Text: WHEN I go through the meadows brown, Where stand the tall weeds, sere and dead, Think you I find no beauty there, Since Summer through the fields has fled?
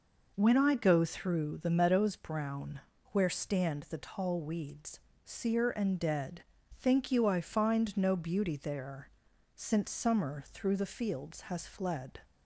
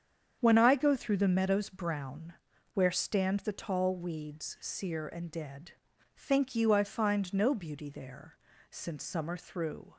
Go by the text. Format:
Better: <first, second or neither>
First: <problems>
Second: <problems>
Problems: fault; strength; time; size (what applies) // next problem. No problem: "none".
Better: first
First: none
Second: starts louder than the rest; strong; until 1.4 s; 8 dB // stops before "the fields has fled"; at 9.9 s